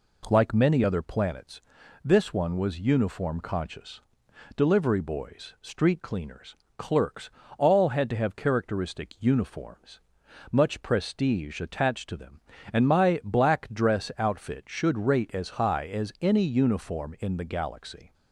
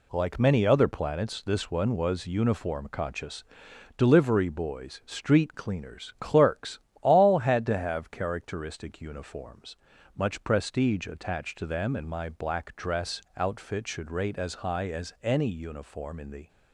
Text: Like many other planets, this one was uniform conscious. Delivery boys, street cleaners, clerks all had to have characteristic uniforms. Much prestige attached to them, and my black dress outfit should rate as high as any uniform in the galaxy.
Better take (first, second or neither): first